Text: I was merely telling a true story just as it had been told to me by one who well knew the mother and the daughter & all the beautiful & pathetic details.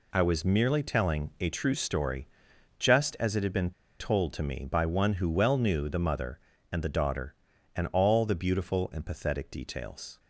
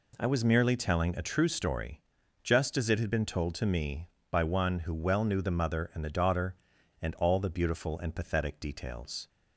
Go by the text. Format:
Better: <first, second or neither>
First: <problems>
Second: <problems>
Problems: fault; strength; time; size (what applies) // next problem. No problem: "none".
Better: second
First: pauses between "story" and "just"; noticeable; at 2.2 s; 0.52 s long // pauses between "been" and "told"; slight; at 3.7 s; 0.28 s long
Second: pauses between "story" and "just"; at 2.0 s; 0.44 s long